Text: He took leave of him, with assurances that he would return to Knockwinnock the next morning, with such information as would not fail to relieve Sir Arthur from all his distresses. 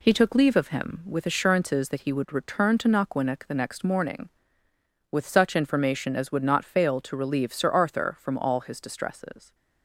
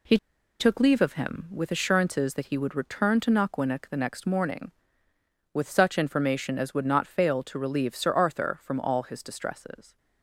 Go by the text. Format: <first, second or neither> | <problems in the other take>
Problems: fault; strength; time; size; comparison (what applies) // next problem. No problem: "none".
first | pauses between "He" and "took"; at 0.1 s; 0.43 s long